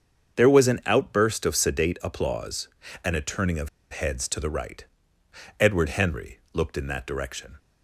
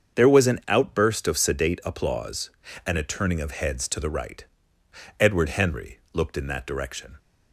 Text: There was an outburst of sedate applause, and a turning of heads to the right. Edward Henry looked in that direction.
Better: second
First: starts louder than the rest; until 1.4 s; 7 dB // pauses between "of" and "heads"; slight; at 3.6 s; 0.22 s long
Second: starts louder than the rest; until 1.2 s; 7 dB

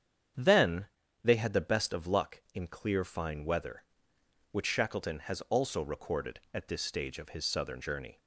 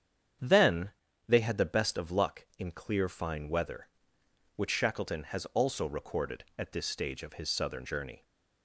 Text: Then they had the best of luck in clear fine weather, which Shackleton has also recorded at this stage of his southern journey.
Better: neither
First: starts louder than the rest; strong; until 1.7 s; 8 dB // pauses between "Then" and "they"; slight; at 0.8 s; 0.36 s long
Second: starts louder than the rest; strong; until 1.7 s; 8 dB // pauses between "Then" and "they"; slight; at 0.9 s; 0.36 s long

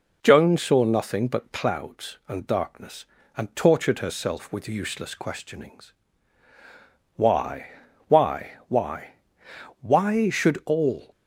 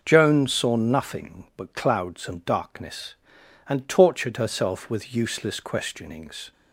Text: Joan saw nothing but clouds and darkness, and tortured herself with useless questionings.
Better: second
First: goes on to say "Why why why why should all"; strong; from 7.1 s on; 3.9 s long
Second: none

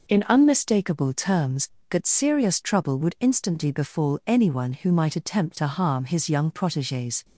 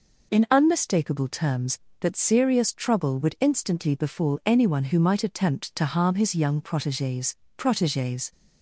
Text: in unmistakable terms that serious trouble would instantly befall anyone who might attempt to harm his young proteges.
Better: first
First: none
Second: says "proteges" twice; at 7.5 s

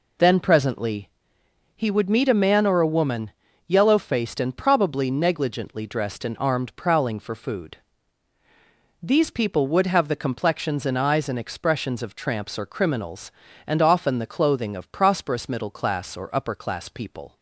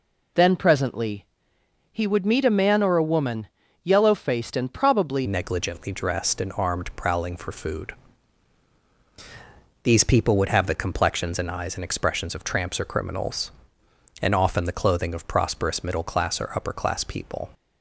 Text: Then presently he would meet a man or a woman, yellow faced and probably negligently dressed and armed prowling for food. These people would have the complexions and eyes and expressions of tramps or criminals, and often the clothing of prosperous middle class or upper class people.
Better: first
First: pauses between "presently" and "he"; noticeable; at 1.0 s; 0.66 s long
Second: pauses between "presently" and "he"; noticeable; at 1.2 s; 0.66 s long // changes voice at "negligently"; from 5.2 s on; 12.3 s long

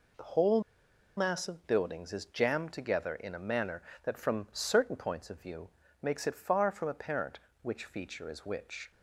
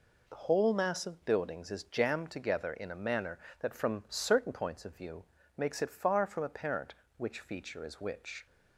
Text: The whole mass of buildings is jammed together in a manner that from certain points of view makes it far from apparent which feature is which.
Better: second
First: pauses between "whole" and "mass"; noticeable; at 0.6 s; 0.56 s long // pauses between "view" and "makes"; slight; at 5.7 s; 0.32 s long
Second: pauses between "view" and "makes"; slight; at 5.2 s; 0.32 s long

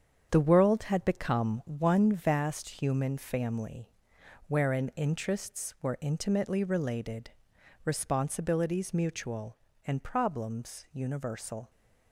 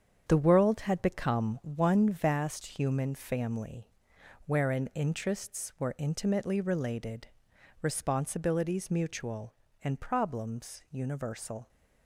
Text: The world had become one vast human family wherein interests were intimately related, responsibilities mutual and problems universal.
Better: neither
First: starts louder than the rest; strong; until 1.3 s; 7.5 dB // pauses between "family" and "wherein"; noticeable; at 3.8 s; 0.58 s long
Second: starts louder than the rest; strong; until 1.2 s; 7.5 dB // pauses between "family" and "wherein"; noticeable; at 3.8 s; 0.58 s long

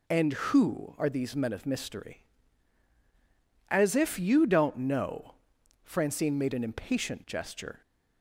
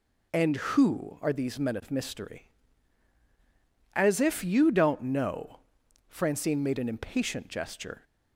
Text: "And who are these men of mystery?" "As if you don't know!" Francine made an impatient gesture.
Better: neither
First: none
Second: none

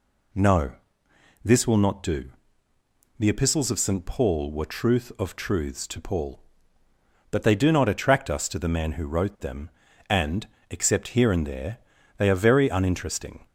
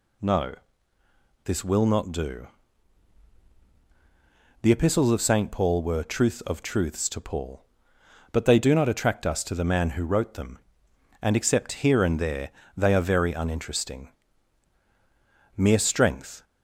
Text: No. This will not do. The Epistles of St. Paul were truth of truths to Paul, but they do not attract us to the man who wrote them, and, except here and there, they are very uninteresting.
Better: first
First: none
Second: goes on to say "Mere strength"; noticeable; from 15.5 s on; 0.86 s long

